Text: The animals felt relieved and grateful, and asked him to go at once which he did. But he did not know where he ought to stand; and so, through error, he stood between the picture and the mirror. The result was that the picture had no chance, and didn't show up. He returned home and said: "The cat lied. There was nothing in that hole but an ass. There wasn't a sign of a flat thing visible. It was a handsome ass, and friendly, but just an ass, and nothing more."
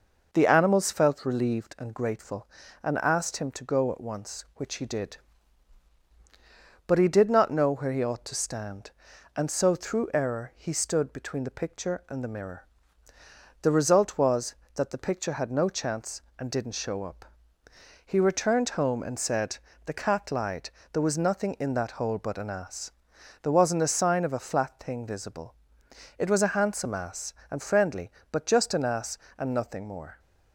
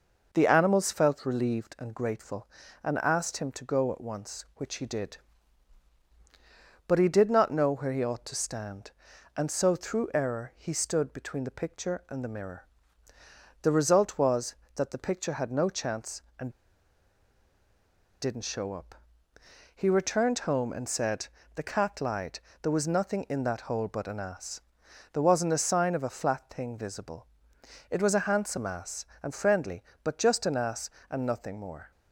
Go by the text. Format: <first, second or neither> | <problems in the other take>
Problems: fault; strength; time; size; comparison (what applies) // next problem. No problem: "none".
first | pauses between "and" and "didn't"; strong; at 16.5 s; 1.7 s long